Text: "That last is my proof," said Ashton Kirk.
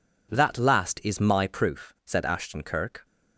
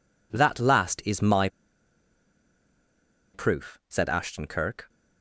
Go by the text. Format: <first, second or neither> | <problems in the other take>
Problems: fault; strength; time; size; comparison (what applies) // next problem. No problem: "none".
first | pauses between "my" and "proof"; strong; at 1.4 s; 1.8 s long